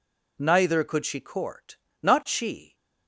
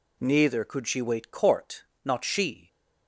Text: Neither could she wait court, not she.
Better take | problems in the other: second | skips "wait"; at 1.2 s

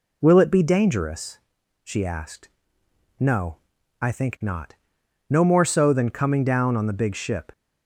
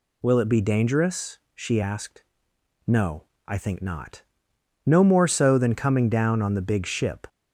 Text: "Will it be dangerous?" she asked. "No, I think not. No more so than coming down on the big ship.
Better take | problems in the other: neither | none

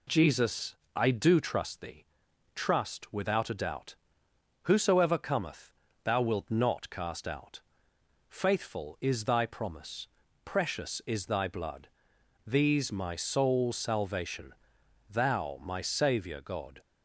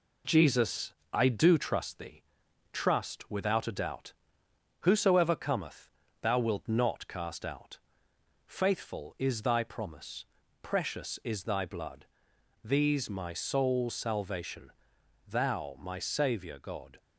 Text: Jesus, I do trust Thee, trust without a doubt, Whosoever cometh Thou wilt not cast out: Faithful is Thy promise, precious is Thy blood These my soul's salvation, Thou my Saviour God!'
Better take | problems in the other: first | gets quieter; slight; throughout; 2.5 dB // pauses between "cometh" and "Thou"; slight; at 5.8 s; 0.34 s long; slight in the first // pauses between "blood" and "These"; noticeable; at 12.0 s; 0.58 s long; noticeable in the first

